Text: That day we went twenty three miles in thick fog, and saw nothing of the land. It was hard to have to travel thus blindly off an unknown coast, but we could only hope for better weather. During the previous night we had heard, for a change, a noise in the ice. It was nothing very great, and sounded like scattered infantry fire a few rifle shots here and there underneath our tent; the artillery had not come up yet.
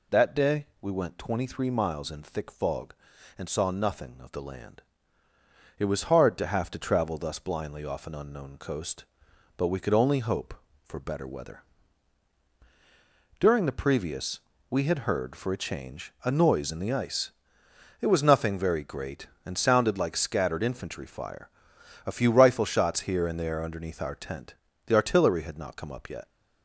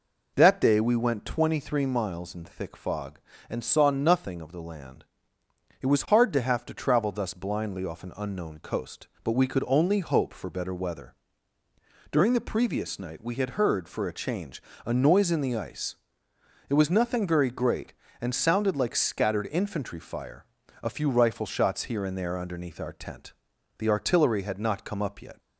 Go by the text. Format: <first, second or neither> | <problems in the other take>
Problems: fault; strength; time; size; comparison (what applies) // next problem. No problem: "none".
second | skips "night"; at 14.5 s // pauses between "fire" and "a"; noticeable; at 21.4 s; 0.58 s long; slight in the second